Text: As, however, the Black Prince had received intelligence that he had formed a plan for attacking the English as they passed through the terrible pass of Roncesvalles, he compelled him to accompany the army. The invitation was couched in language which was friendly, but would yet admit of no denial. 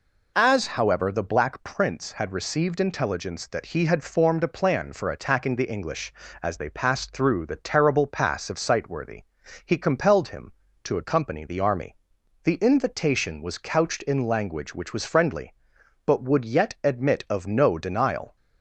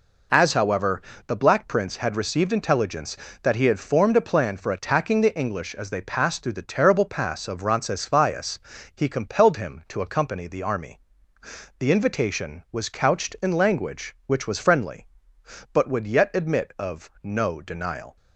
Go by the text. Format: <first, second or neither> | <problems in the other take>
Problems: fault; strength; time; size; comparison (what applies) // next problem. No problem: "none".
second | says "Sightworthy" for "Roncesvalles"; at 8.5 s